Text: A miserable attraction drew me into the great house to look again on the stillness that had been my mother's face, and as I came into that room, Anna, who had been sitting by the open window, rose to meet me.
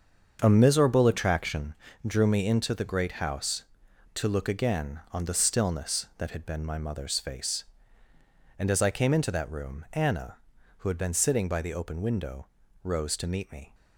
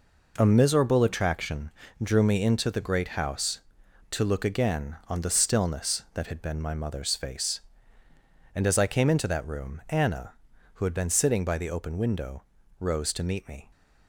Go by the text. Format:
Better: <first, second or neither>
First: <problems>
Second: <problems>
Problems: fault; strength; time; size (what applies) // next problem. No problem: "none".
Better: second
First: starts louder than the rest; until 1.7 s; 7 dB // pauses between "attraction" and "drew"; slight; at 1.7 s; 0.32 s long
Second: pauses between "attraction" and "drew"; slight; at 1.7 s; 0.32 s long